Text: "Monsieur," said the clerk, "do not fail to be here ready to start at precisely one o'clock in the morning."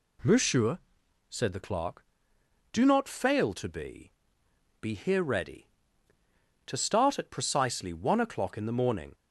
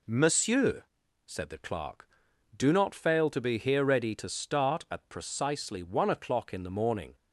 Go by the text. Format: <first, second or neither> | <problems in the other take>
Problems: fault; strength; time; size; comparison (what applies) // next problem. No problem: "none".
second | says "be" twice; at 4.8 s